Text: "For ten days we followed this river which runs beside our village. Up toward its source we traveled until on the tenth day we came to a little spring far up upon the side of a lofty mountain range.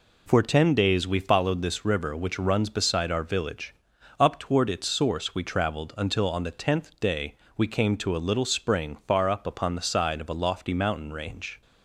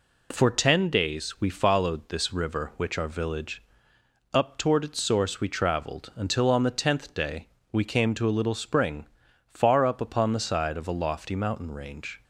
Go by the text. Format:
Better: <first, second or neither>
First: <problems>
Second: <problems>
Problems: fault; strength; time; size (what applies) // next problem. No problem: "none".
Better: first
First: pauses between "day" and "we"; slight; at 7.3 s; 0.18 s long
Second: skips "runs beside"; at 2.9 s // pauses between "day" and "we"; slight; at 7.4 s; 0.24 s long // pauses between "spring" and "far"; at 9.0 s; 0.42 s long